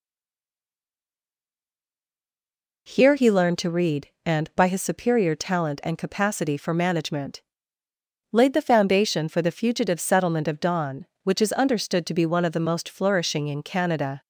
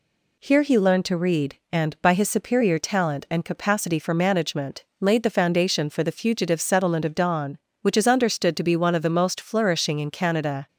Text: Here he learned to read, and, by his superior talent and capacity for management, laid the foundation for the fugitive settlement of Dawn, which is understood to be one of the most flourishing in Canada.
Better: second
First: stays silent before the first word; strong; until 2.8 s; 2.8 s long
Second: none

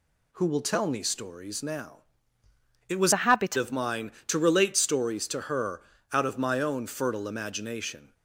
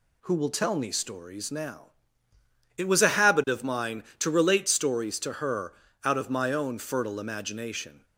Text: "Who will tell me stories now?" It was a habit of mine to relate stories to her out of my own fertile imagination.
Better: second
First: changes voice from "a" to "habit"; from 3.1 to 3.5 s; 0.4 s long // pauses between "her" and "out"; slight; at 5.8 s; 0.32 s long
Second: pauses between "her" and "out"; slight; at 5.7 s; 0.32 s long

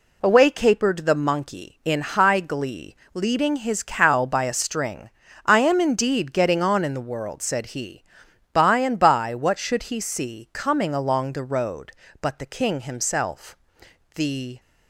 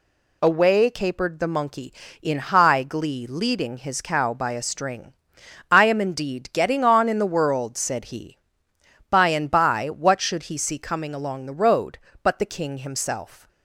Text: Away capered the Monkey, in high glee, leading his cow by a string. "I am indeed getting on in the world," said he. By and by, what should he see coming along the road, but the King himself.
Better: second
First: goes on to say "The"; slight; from 14.1 s on; 0.44 s long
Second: none

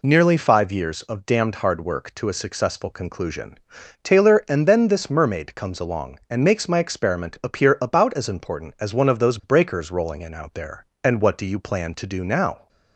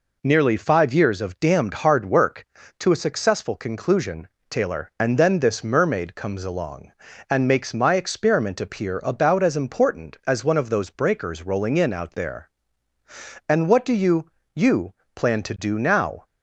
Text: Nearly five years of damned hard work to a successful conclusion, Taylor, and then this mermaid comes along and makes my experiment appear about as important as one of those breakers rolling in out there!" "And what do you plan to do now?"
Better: first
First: none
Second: says "you" twice; at 14.5 s

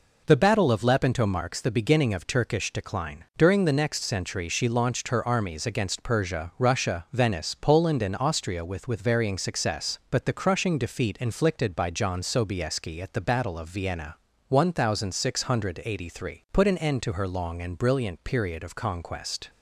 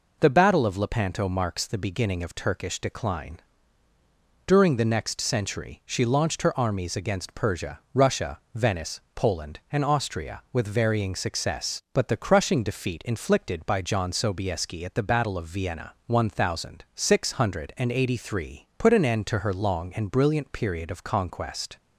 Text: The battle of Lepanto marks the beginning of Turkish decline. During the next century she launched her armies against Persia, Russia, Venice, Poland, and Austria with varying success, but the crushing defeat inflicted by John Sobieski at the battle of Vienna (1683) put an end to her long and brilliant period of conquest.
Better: second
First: says "with" twice; at 8.8 s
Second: none

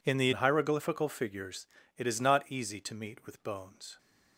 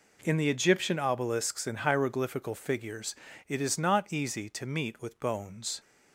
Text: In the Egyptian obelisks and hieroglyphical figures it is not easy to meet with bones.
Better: second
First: skips "Egyptian obelisks and"; at 0.3 s // pauses between "figures" and "it"; slight; at 1.6 s; 0.32 s long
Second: pauses between "figures" and "it"; slight; at 3.1 s; 0.34 s long

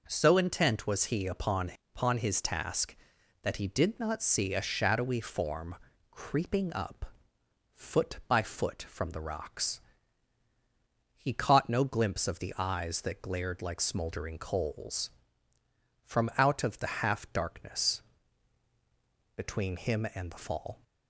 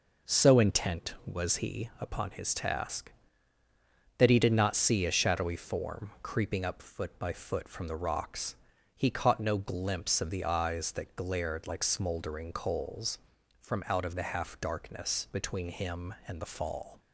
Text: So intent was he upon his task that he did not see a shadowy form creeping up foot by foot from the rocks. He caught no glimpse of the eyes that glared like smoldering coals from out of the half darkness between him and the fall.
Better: second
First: says "upon" twice; at 1.9 s // pauses between "form" and "creeping"; slight; at 5.7 s; 0.36 s long // pauses between "up" and "foot"; noticeable; at 7.0 s; 0.68 s long // pauses between "darkness" and "between"; strong; at 18.0 s; 1.3 s long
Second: none

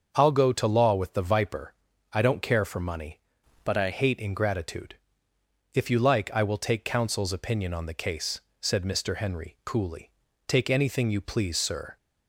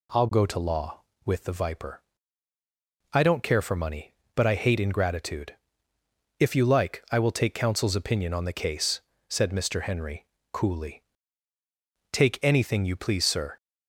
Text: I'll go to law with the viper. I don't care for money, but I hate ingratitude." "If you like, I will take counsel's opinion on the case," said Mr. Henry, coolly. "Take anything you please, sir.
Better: second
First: starts louder than the rest; until 1.1 s; 6.5 dB // changes voice from "but" to "I"; from 3.6 to 3.9 s; 0.3 s long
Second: none

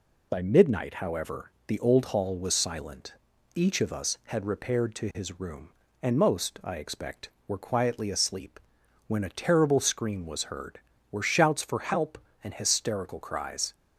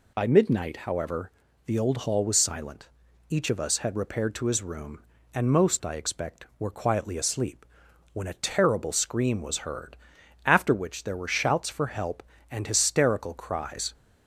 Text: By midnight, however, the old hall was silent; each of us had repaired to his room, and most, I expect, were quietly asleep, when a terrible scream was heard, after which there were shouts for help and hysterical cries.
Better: second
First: skips "after which there"; at 10.9 s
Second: none

